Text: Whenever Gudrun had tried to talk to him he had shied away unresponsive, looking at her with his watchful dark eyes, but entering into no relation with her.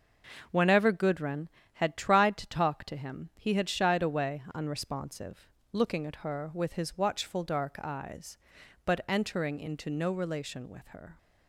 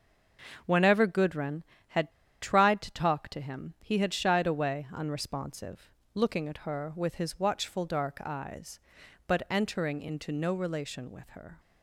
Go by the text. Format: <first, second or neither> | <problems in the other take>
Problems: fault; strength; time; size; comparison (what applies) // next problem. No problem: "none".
first | starts louder than the rest; until 1.6 s; 6 dB // pauses between "had" and "tried"; slight; at 2.1 s; 0.29 s long